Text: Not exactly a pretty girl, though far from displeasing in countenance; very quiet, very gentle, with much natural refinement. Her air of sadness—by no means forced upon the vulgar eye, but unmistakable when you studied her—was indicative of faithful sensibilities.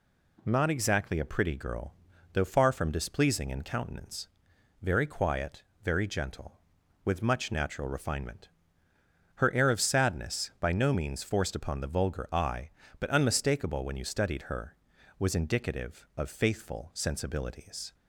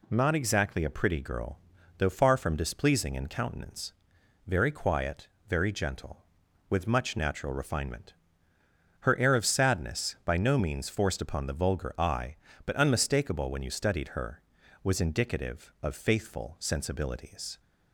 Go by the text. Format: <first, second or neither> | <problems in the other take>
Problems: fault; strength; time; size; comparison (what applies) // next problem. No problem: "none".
neither | none